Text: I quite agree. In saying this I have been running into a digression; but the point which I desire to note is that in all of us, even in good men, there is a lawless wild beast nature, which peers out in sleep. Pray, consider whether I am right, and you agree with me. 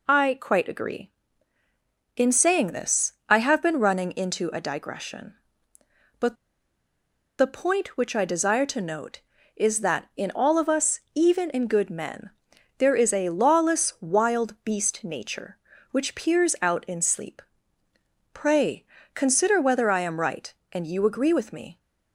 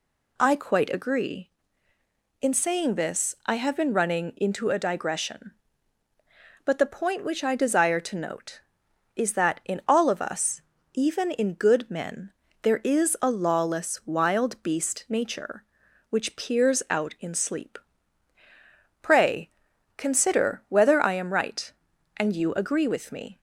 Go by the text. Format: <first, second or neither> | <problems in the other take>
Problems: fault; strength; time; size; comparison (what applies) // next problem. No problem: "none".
second | pauses between "this" and "I"; slight; at 3.1 s; 0.16 s long // pauses between "but" and "the"; at 6.3 s; 1.0 s long